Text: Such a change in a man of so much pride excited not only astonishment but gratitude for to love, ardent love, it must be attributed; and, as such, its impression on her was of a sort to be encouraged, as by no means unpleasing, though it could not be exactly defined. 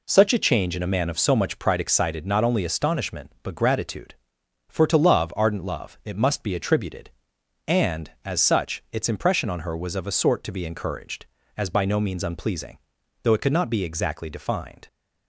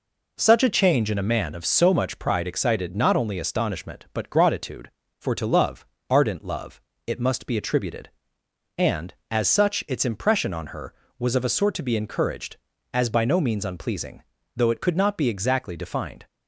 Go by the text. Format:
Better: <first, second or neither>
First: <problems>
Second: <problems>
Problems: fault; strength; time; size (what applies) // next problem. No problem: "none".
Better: neither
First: none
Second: none